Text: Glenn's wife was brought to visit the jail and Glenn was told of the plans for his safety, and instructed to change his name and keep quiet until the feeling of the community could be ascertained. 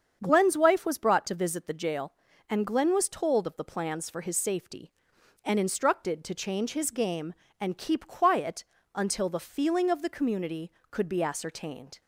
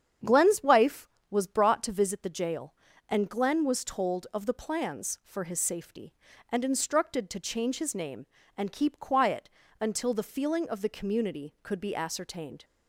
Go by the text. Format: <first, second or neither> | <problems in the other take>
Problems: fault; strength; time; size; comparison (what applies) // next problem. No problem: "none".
second | starts louder than the rest; strong; until 1.2 s; 7.5 dB; strong in the second // says "game" for "name"; at 6.9 s // pauses between "quiet" and "until"; slight; at 8.6 s; 0.32 s long; slight in the second